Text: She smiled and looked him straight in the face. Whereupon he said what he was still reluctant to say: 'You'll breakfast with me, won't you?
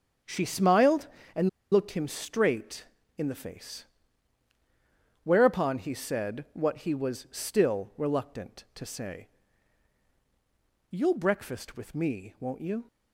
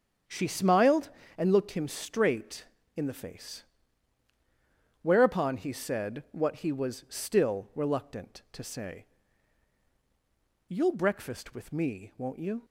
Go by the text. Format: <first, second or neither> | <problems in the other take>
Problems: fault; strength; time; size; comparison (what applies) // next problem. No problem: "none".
second | starts louder than the rest; strong; until 1.7 s; 8 dB; strong in the second // pauses between "and" and "looked"; slight; at 1.4 s; 0.22 s long